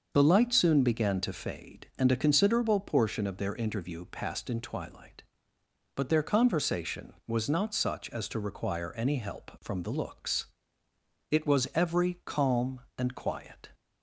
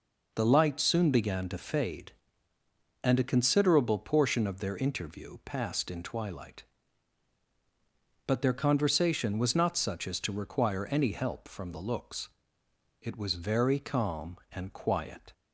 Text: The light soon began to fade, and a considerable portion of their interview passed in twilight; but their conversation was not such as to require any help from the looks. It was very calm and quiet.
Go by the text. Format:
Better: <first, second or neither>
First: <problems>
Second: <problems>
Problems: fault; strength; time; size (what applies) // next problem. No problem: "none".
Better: second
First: starts louder than the rest; until 1.1 s; 6.5 dB // says "every" for "very"; at 11.7 s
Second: none